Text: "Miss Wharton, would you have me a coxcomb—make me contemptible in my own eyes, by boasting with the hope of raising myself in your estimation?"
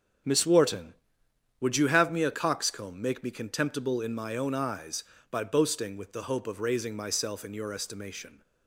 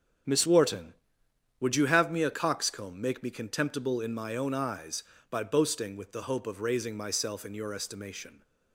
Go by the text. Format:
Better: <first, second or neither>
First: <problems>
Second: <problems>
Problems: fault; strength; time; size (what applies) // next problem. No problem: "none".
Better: neither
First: starts louder than the rest; strong; until 1.9 s; 7.5 dB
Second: starts louder than the rest; strong; until 1.9 s; 8.5 dB